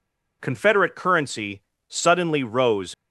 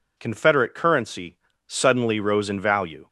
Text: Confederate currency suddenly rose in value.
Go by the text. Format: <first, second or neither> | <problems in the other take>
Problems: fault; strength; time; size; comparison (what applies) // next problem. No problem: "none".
second | pauses between "currency" and "suddenly"; slight; at 1.6 s; 0.26 s long; slight in the second // stops before "in value"; at 2.9 s